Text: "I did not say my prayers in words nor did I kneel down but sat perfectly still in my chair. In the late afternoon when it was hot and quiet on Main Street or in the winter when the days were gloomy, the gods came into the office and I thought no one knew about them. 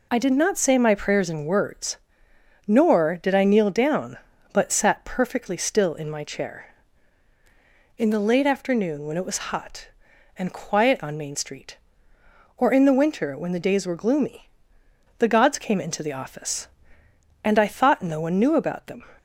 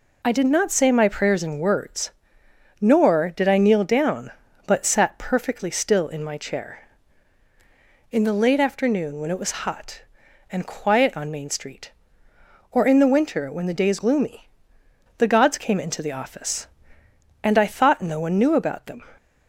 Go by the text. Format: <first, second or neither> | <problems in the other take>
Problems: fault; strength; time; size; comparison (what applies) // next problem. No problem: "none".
first | pauses between "words" and "nor"; noticeable; at 2.1 s; 0.70 s long; noticeable in the first // skips "were"; at 13.9 s